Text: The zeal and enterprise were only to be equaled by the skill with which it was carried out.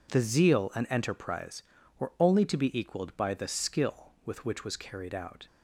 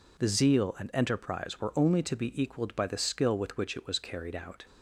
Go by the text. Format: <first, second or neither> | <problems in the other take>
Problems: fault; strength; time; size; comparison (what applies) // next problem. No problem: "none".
second | skips "it"; at 4.6 s